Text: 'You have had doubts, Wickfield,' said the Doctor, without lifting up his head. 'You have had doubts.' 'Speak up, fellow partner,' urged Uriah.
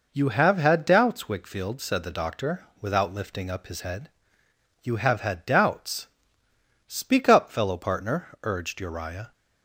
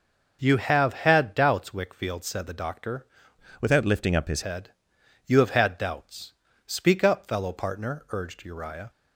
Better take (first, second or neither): first